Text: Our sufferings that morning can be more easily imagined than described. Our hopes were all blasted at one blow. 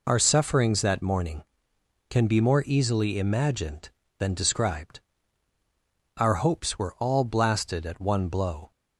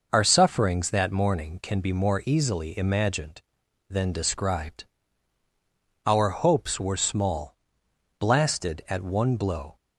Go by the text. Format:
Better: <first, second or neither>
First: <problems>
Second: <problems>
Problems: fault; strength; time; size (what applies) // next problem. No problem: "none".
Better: first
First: none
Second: says "small" for "all"; at 6.9 s